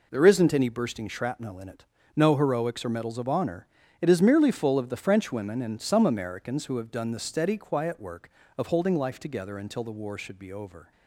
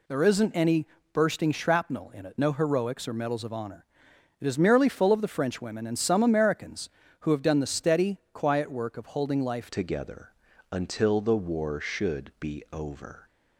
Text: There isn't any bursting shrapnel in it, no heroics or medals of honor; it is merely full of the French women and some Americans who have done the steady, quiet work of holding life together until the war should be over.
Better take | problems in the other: first | pauses between "any" and "bursting"; slight; at 0.8 s; 0.28 s long // changes voice at "together"; from 9.7 s on; 3.5 s long // pauses between "together" and "until"; at 10.3 s; 0.38 s long

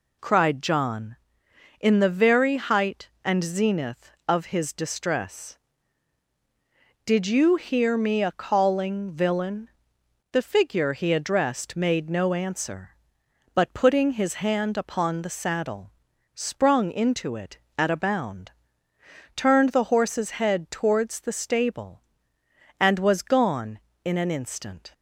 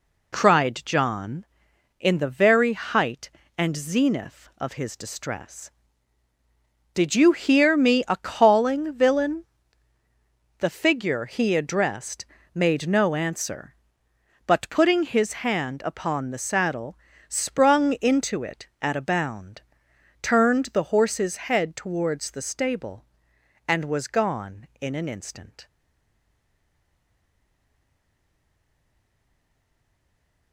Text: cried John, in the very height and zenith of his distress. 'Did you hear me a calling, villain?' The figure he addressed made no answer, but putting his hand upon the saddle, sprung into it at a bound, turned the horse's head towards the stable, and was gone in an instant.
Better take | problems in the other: first | pauses between "addressed" and "made"; slight; at 12.2 s; 0.28 s long // stays silent after the last word; strong; from 25.6 s on; 4.9 s long

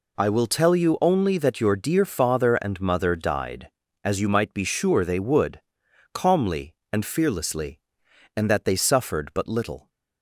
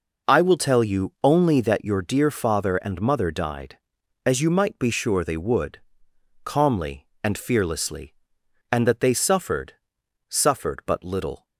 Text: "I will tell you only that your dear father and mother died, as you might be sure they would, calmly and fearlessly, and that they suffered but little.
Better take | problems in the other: first | says "suffered" twice; at 10.2 s

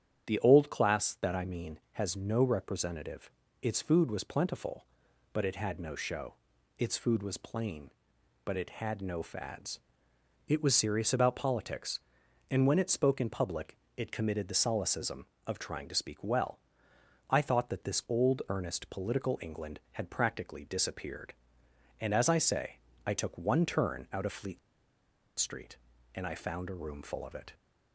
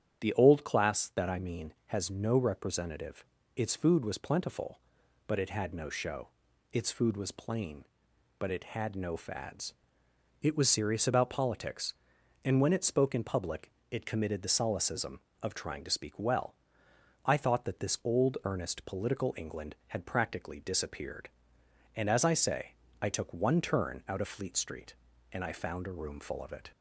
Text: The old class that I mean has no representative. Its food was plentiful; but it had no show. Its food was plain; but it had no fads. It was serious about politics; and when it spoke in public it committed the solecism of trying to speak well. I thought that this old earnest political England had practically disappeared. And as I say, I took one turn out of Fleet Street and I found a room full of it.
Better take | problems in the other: second | starts louder than the rest; strong; until 1.3 s; 9 dB; strong in the second // pauses between "public" and "it"; slight; at 13.7 s; 0.20 s long; slight in the second // pauses between "Fleet" and "Street"; noticeable; at 24.5 s; 0.80 s long

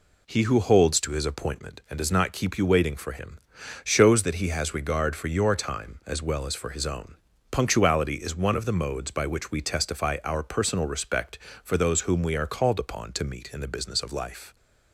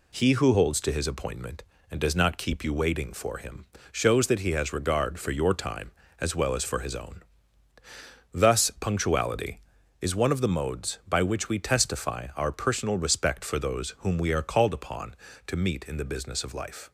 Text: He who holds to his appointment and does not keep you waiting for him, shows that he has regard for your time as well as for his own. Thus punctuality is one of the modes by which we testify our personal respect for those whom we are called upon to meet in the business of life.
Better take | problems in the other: second | skips "Thus"; at 7.3 s

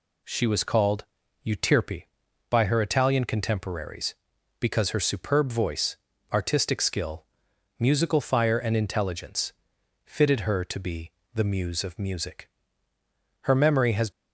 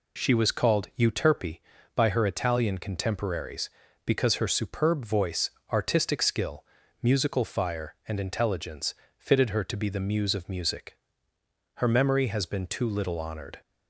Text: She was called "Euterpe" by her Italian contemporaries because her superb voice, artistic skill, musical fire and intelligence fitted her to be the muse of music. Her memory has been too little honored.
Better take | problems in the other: second | pauses between "called" and "Euterpe"; at 1.0 s; 0.40 s long // pauses between "intelligence" and "fitted"; noticeable; at 9.5 s; 0.52 s long; slight in the second // pauses between "be" and "the"; slight; at 11.1 s; 0.24 s long // stops before "been too little honored"; at 14.1 s

